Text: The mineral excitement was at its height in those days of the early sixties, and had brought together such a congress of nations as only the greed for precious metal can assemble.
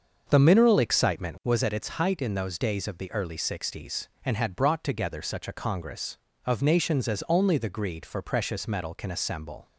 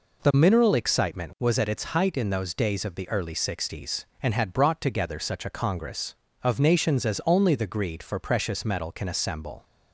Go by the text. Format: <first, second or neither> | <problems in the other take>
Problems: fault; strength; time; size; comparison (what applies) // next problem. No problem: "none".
second | starts louder than the rest; until 1.7 s; 6.5 dB